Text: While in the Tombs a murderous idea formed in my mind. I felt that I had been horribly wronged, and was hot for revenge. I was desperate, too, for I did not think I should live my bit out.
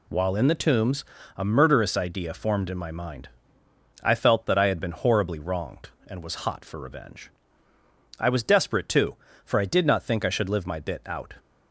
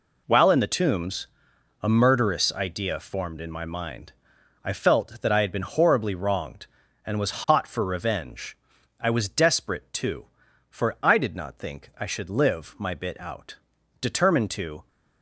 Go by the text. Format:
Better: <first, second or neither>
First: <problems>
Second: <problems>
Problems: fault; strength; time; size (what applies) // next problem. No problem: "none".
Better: first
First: pauses between "Tombs" and "a"; slight; at 1.0 s; 0.32 s long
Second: pauses between "Tombs" and "a"; noticeable; at 1.2 s; 0.54 s long // goes on to say "Determined to"; noticeable; from 14.0 s on; 0.86 s long